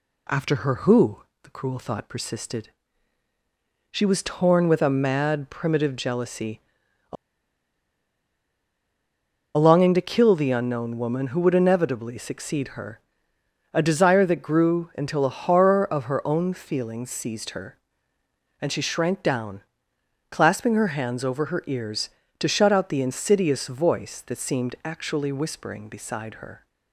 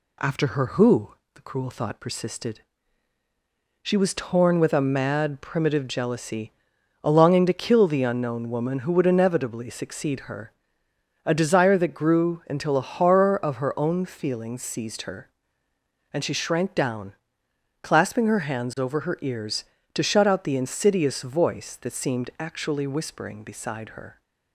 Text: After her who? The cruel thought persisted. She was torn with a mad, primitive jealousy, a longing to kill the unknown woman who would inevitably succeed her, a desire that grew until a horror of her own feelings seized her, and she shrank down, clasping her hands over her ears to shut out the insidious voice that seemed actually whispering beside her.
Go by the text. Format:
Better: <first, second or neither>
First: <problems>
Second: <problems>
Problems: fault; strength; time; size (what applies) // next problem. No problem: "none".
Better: second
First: pauses between "a" and "longing"; strong; at 7.1 s; 2.4 s long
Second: none